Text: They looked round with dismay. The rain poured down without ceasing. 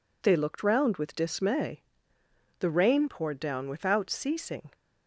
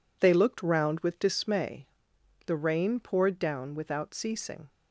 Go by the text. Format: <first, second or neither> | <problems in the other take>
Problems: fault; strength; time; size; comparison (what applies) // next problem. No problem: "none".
neither | none